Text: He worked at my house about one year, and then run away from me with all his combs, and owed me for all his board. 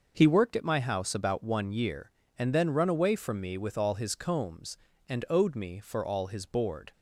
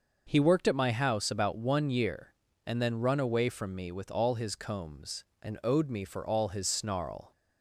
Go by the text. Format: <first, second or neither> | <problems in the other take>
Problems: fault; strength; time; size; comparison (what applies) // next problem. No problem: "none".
first | starts louder than the rest; noticeable; until 1.2 s; 6 dB // says "snarl" for "board"; at 6.6 s